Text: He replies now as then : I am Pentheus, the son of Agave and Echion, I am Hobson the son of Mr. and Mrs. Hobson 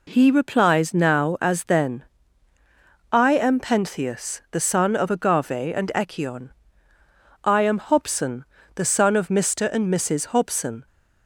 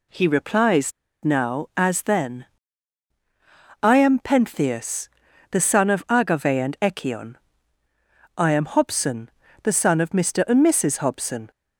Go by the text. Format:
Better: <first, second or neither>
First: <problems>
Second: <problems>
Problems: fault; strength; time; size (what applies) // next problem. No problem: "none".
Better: first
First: pauses between "Hobson" and "the"; slight; at 8.4 s; 0.32 s long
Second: pauses between "replies" and "now"; slight; at 0.9 s; 0.32 s long // pauses between "Hobson" and "the"; slight; at 9.2 s; 0.34 s long